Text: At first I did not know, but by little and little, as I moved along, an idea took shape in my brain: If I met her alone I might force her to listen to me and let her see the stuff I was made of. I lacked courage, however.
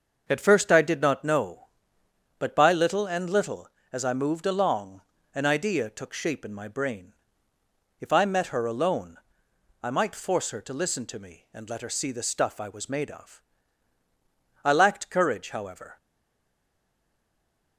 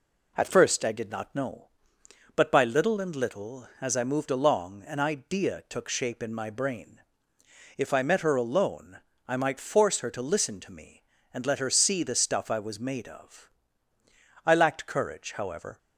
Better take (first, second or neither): second